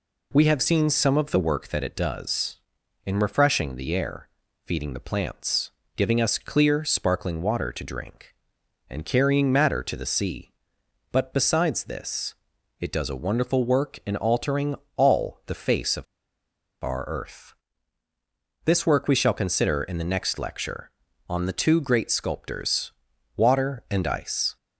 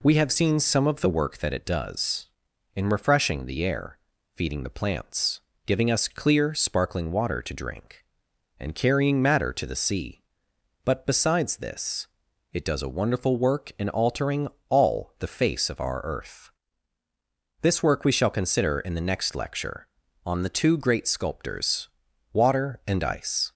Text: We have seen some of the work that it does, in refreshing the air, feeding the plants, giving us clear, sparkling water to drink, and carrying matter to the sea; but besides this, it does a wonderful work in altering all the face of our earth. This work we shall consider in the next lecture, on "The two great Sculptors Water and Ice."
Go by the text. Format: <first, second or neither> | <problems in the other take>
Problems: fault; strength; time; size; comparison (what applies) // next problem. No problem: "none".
second | pauses between "altering" and "all"; slight; at 14.7 s; 0.22 s long; slight in the second // pauses between "of" and "our"; noticeable; at 16.0 s; 0.78 s long // pauses between "Sculptors" and "Water"; at 22.9 s; 0.42 s long; also in the second